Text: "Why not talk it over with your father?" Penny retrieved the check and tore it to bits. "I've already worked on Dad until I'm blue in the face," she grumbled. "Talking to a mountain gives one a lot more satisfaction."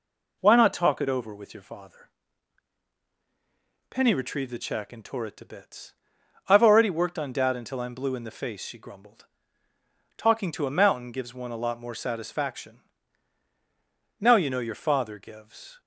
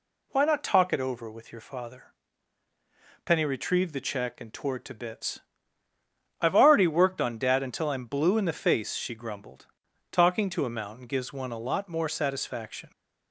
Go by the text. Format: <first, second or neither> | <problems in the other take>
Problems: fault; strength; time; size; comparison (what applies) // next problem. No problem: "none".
second | goes on to say "Now you know your father gives"; from 14.2 s on; 1.6 s long